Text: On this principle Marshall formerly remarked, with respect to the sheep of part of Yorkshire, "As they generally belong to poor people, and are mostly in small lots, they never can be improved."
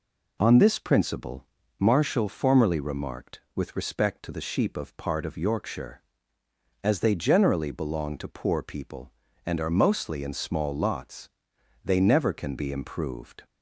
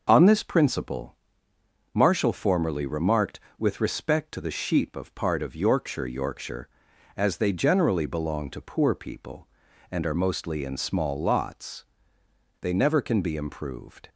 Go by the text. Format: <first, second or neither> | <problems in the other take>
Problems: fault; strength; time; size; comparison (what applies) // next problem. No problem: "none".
first | pauses between "principle" and "Marshall"; noticeable; at 1.1 s; 0.78 s long; slight in the first // says "Yorkshire" twice; at 6.0 s